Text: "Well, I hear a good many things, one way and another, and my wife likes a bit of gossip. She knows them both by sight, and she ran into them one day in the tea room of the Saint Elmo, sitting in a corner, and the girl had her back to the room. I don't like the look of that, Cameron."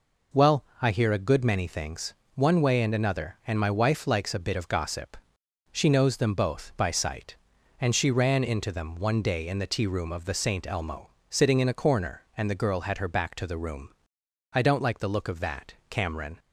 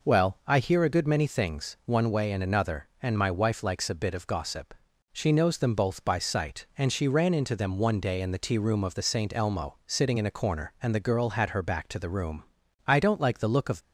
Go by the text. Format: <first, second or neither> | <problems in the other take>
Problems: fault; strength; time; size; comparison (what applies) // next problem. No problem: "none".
first | stops before "that Cameron"; at 13.8 s